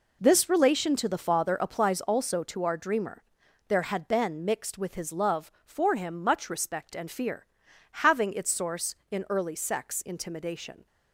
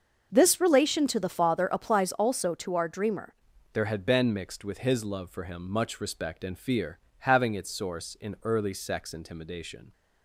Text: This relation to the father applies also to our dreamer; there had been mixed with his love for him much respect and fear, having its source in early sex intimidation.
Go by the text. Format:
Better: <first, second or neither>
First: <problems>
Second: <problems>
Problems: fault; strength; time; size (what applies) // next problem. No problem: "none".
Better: first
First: none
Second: starts louder than the rest; until 1.3 s; 6.5 dB // changes voice at "there"; from 3.7 s on; 6.2 s long